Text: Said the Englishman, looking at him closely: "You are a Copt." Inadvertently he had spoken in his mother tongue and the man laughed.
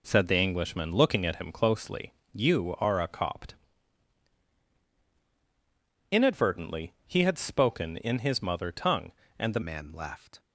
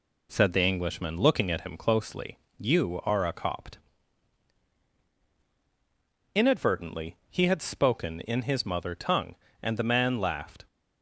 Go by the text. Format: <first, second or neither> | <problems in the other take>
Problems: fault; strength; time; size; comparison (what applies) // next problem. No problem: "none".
second | changes voice at "man"; from 9.6 s on; 0.7 s long